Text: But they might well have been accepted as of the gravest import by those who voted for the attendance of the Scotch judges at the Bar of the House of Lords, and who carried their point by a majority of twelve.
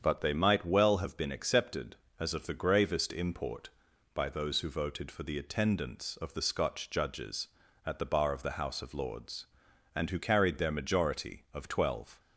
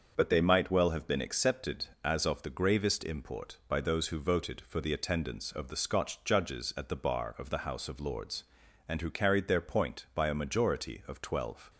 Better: second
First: starts louder than the rest; strong; until 1.0 s; 7.5 dB // skips "point by a"; at 10.7 s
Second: starts louder than the rest; until 1.1 s; 6.5 dB

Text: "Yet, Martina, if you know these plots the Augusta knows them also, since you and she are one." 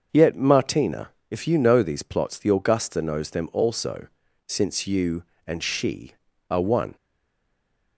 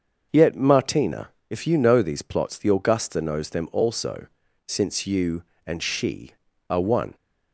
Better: second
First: starts louder than the rest; until 1.3 s; 6.5 dB // stays silent after the last word; from 6.9 s on; 1.0 s long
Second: starts louder than the rest; until 1.5 s; 6.5 dB

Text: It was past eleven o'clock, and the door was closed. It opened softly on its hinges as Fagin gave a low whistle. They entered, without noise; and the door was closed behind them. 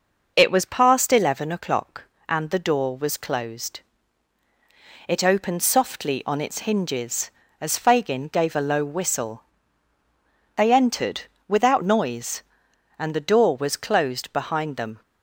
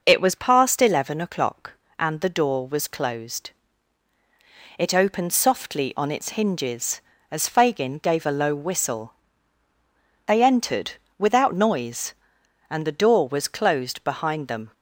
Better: neither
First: none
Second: none

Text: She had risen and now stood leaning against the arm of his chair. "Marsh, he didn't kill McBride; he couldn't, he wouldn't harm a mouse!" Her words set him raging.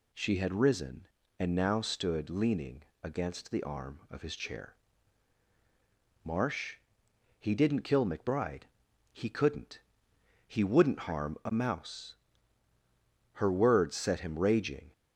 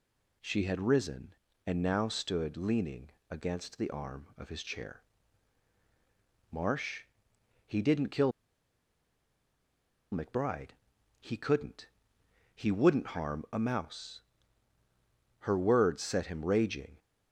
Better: first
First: pauses between "leaning" and "against"; slight; at 2.8 s; 0.20 s long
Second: pauses between "leaning" and "against"; slight; at 3.1 s; 0.20 s long // pauses between "kill" and "McBride"; strong; at 8.3 s; 1.8 s long

